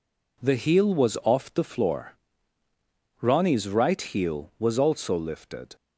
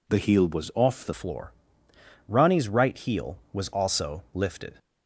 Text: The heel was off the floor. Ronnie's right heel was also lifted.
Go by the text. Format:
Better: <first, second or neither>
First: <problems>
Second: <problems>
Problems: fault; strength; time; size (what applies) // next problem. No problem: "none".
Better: first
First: none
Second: changes voice at "floor"; from 1.1 s on; 3.6 s long